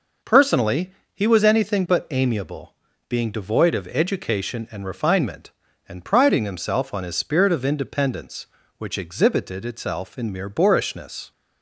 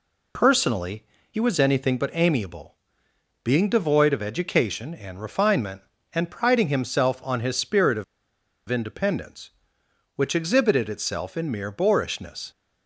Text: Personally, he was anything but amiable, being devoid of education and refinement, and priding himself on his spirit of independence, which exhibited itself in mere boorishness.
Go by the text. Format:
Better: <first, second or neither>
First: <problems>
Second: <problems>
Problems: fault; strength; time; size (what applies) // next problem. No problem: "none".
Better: first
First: none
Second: pauses between "of" and "independence"; noticeable; at 8.0 s; 0.64 s long